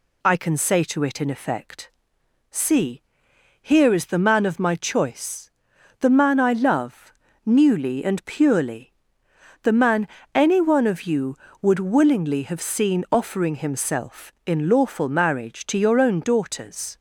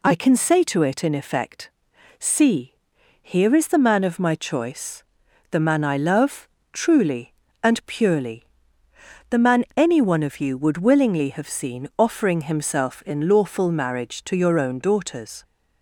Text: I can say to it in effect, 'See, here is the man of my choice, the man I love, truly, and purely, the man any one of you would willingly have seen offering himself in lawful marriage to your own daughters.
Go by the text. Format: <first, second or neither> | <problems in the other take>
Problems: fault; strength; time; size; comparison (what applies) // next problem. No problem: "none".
second | says "newly" for "truly"; at 7.4 s // pauses between "man" and "any"; slight; at 10.0 s; 0.28 s long